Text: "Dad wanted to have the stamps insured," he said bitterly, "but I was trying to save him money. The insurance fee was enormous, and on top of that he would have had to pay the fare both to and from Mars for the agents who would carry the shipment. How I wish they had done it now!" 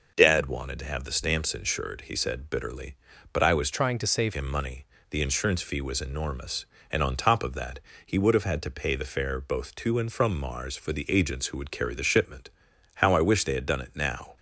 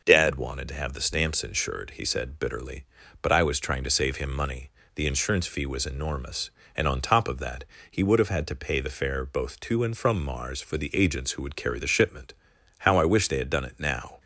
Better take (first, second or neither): second